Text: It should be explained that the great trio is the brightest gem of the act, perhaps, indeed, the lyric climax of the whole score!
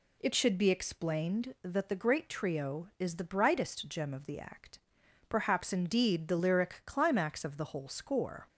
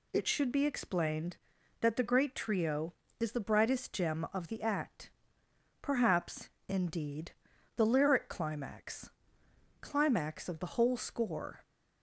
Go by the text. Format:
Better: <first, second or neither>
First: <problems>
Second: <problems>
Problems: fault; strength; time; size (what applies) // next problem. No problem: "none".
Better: first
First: none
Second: says "climax" twice; at 9.8 s